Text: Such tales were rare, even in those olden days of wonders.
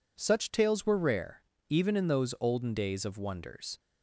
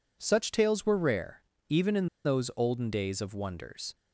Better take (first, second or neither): first